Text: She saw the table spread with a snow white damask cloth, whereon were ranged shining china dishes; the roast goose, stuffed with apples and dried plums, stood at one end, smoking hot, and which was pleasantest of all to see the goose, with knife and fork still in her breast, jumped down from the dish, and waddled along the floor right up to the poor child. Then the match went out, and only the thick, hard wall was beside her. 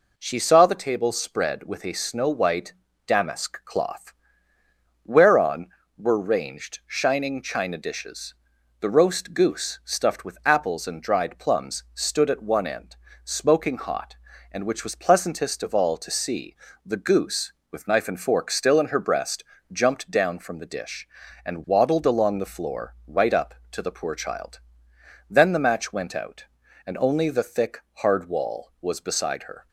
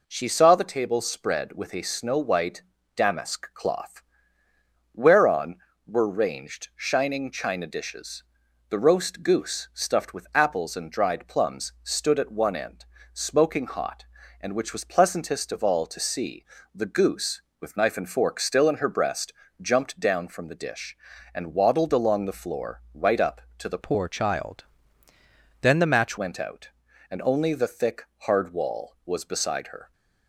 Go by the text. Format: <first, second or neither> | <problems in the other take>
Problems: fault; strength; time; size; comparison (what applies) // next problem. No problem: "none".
first | pauses between "white" and "damask"; slight; at 2.6 s; 0.32 s long; slight in the first // pauses between "see" and "the"; slight; at 16.4 s; 0.28 s long; slight in the first // changes voice from "poor" to "match"; from 23.8 to 26.1 s; 2.3 s long